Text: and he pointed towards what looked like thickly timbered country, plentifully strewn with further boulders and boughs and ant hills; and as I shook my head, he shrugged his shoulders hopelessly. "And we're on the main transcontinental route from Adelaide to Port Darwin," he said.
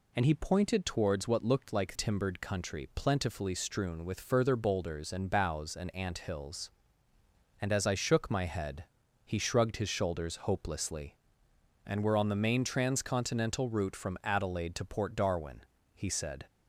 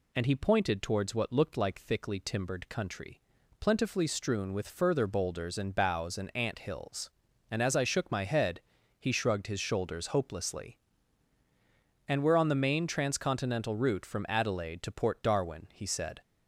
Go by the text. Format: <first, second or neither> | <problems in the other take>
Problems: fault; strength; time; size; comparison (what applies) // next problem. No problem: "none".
second | skips "thickly"; at 1.9 s